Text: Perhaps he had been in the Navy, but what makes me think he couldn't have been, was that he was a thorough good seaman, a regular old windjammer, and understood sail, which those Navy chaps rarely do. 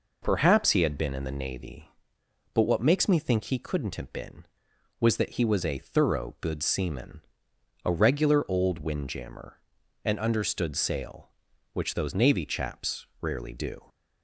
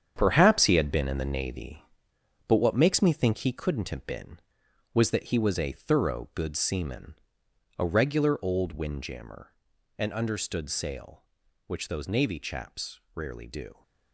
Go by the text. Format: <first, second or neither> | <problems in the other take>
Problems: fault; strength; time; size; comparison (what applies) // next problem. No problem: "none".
first | gets quieter; strong; throughout; 8.5 dB // pauses between "chaps" and "rarely"; slight; at 12.9 s; 0.16 s long; slight in the first